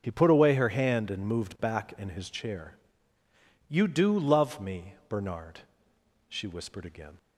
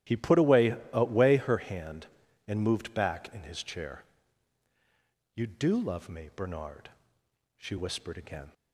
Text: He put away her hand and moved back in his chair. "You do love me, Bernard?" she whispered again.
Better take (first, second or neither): first